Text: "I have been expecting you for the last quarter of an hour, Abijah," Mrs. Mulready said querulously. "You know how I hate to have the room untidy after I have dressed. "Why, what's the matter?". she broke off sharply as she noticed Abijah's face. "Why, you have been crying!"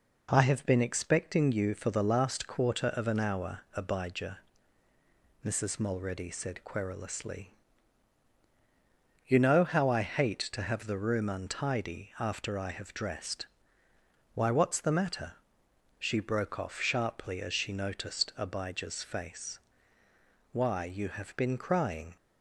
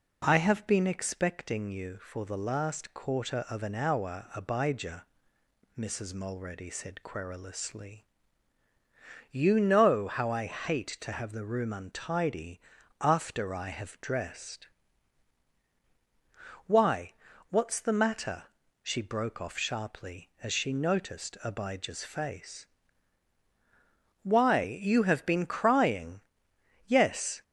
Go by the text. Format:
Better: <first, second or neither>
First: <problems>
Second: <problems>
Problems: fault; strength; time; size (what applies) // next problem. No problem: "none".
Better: first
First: none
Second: pauses between "untidy" and "after"; at 12.6 s; 0.40 s long // goes on to say "Yes"; from 26.8 s on; 0.56 s long